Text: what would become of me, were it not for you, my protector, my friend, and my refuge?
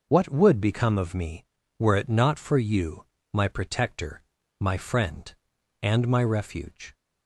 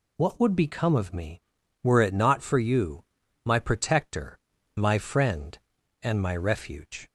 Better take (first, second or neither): neither